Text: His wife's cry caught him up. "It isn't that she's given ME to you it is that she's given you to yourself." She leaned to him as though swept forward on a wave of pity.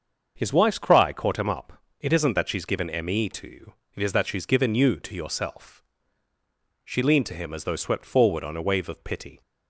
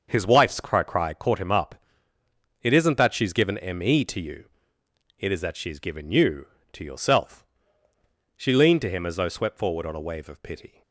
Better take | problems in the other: first | starts louder than the rest; until 1.1 s; 6.5 dB; also in the first // says "cry" twice; at 0.8 s // pauses between "you" and "it"; noticeable; at 4.4 s; 0.74 s long; slight in the first

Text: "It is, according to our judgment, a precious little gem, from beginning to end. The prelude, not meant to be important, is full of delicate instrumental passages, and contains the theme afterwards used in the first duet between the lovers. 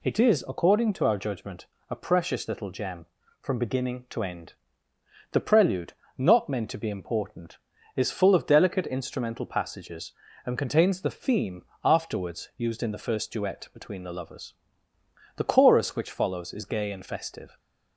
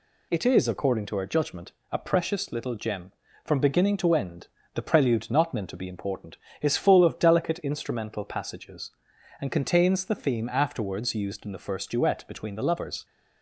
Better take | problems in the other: second | pauses between "theme" and "afterwards"; slight; at 11.6 s; 0.20 s long // goes on to say "The chorus which follows is gay and festive"; strong; from 15.3 s on; 2.2 s long

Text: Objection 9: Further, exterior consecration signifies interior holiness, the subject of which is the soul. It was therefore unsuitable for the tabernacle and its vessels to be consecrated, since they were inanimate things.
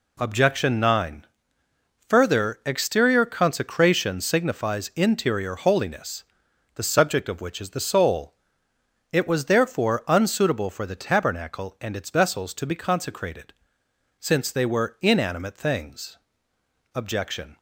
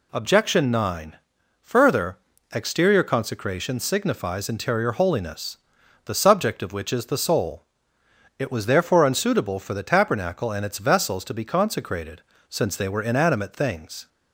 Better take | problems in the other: second | goes on to say "Objection"; noticeable; from 16.9 s on; 0.62 s long

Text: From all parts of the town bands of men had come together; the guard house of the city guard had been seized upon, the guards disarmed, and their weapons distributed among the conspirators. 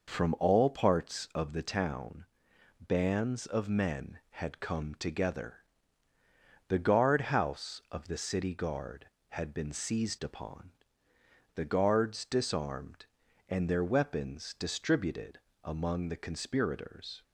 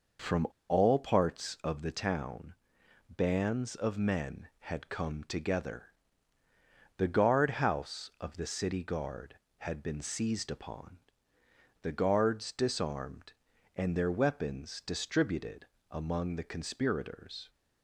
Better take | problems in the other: first | pauses between "From" and "all"; slight; at 0.4 s; 0.23 s long // pauses between "town" and "bands"; noticeable; at 2.5 s; 0.56 s long; noticeable in the first // pauses between "distributed" and "among"; slight; at 15.6 s; 0.24 s long; slight in the first

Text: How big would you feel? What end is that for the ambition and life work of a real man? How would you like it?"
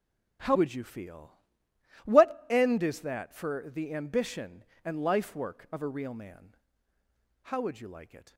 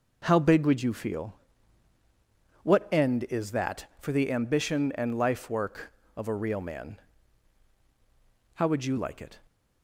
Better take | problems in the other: second | skips "big"; at 0.5 s

